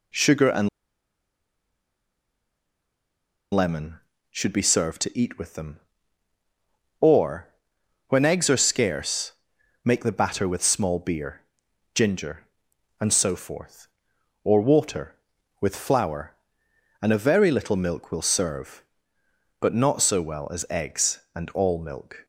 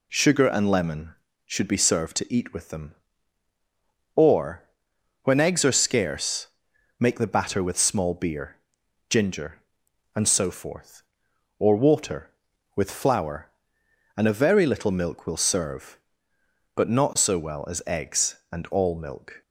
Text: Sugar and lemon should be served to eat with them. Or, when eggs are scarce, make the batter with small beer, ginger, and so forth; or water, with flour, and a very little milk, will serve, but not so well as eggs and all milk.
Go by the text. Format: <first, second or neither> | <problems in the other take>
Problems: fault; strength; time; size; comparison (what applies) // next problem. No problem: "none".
second | pauses between "and" and "lemon"; strong; at 0.6 s; 2.8 s long